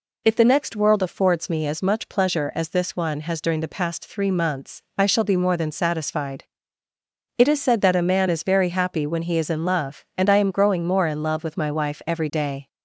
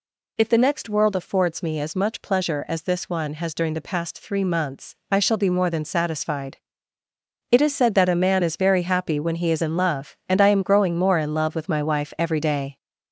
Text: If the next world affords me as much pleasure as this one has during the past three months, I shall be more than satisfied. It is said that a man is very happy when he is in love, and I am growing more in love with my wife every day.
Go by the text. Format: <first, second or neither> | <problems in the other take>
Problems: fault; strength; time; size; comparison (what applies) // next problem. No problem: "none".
first | gets louder; noticeable; throughout; 5.5 dB